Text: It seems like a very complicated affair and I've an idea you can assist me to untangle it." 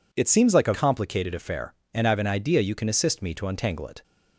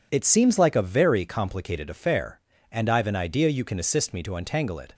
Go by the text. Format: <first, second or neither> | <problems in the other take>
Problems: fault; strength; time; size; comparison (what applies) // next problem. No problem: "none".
second | skips "very"; at 0.7 s